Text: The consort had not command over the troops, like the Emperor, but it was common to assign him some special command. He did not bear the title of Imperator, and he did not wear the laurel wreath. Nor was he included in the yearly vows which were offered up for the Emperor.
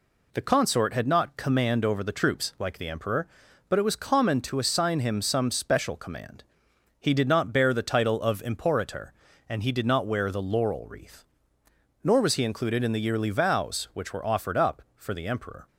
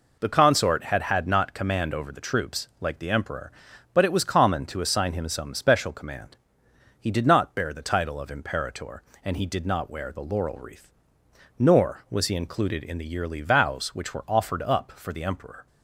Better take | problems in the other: first | says "had" twice; at 1.0 s

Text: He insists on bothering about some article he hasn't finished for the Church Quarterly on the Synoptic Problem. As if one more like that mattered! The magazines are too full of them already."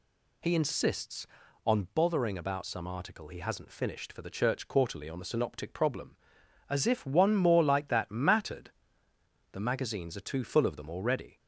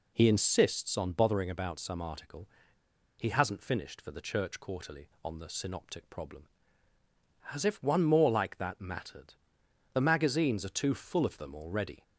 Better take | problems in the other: first | pauses between "article" and "he"; noticeable; at 2.4 s; 0.69 s long

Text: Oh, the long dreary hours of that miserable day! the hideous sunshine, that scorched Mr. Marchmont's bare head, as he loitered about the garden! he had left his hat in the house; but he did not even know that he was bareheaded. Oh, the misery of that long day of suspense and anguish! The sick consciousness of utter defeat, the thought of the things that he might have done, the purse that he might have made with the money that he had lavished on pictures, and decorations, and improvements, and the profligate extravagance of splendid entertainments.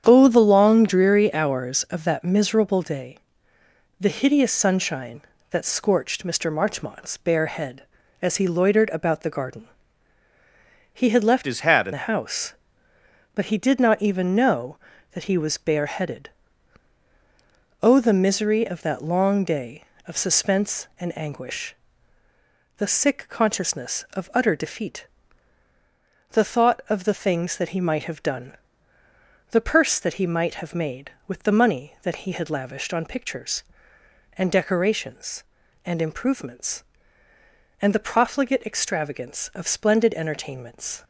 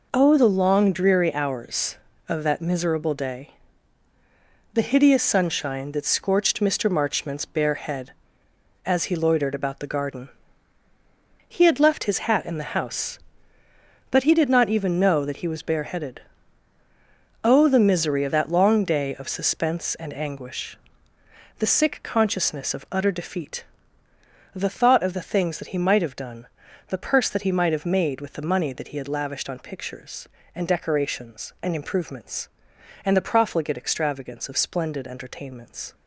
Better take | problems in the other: second | starts louder than the rest; strong; until 1.0 s; 8.5 dB // changes voice from "his" to "in"; from 11.4 to 11.9 s; 0.5 s long

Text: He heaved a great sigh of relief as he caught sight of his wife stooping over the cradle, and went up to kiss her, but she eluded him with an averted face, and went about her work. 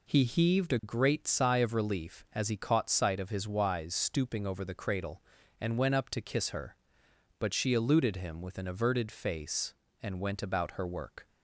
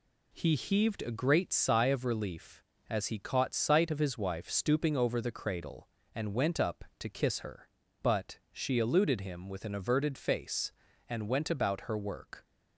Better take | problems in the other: second | says "wise" for "wife"; at 3.4 s

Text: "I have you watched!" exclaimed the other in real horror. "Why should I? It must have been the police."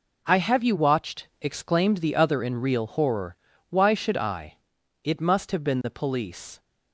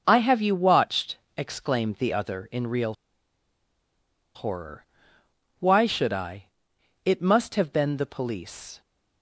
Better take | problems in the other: first | pauses between "real" and "horror"; strong; at 2.9 s; 1.4 s long

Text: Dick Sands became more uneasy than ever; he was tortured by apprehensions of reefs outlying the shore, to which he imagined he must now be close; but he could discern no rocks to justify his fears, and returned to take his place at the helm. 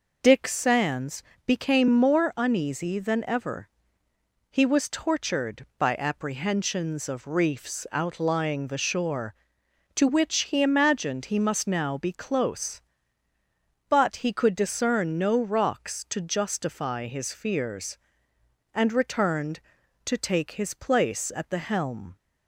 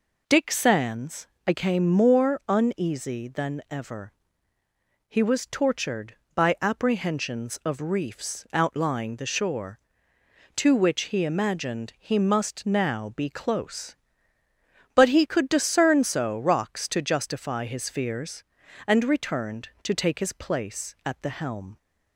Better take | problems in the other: first | pauses between "Sands" and "became"; slight; at 1.2 s; 0.18 s long; slight in the first // says "so" for "no"; at 16.0 s

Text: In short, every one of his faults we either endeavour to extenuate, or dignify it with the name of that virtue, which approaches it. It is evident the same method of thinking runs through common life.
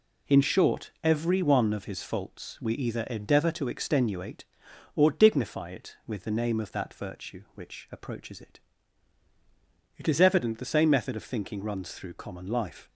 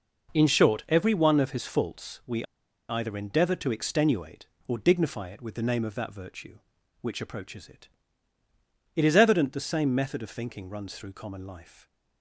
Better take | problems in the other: first | pauses between "we" and "either"; at 2.4 s; 0.45 s long

